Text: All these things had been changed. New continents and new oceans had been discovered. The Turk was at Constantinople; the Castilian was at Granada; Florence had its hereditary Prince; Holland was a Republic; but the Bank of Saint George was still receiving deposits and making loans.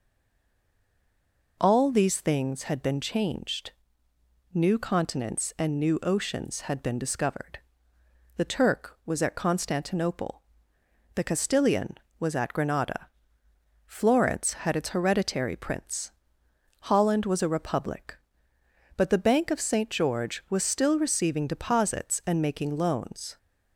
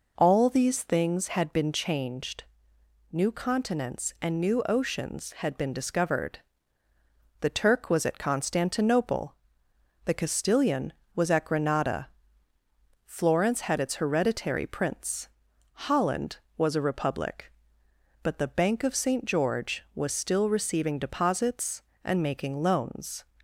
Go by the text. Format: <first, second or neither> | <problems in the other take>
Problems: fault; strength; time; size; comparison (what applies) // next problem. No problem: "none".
second | stays silent before the first word; noticeable; until 1.5 s; 1.5 s long